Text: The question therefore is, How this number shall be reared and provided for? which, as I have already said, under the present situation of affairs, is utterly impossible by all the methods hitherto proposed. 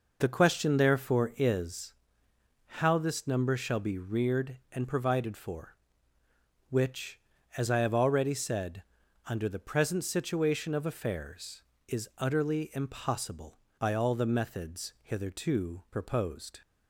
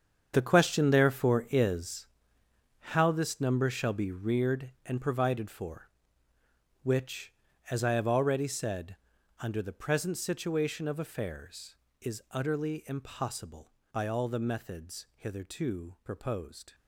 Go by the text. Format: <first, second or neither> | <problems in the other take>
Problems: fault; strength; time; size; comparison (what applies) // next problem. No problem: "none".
first | gets quieter; strong; throughout; 13.5 dB